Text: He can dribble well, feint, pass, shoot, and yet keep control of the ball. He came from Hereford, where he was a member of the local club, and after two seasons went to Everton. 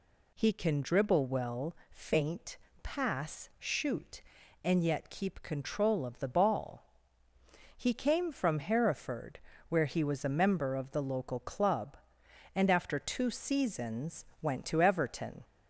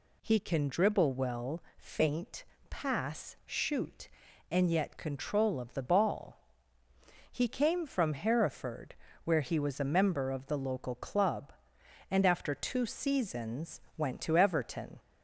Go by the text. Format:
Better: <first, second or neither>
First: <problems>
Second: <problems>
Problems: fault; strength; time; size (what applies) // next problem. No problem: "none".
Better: first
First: pauses between "seasons" and "went"; slight; at 14.2 s; 0.16 s long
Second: skips "keep"; at 4.9 s // pauses between "seasons" and "went"; slight; at 13.8 s; 0.16 s long